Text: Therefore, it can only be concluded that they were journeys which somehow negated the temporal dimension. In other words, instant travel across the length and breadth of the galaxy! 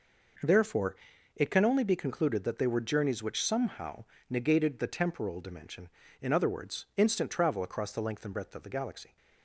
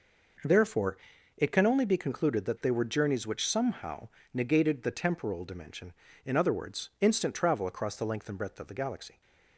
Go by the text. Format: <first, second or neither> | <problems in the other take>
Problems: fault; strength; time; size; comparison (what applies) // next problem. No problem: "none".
neither | pauses between "somehow" and "negated"; slight; the same in both